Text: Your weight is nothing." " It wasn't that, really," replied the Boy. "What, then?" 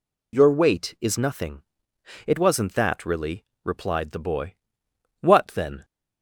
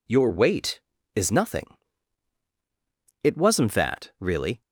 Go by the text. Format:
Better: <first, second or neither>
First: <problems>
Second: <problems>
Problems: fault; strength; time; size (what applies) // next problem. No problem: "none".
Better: first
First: none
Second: stops before "replied the Boy What then"; at 4.6 s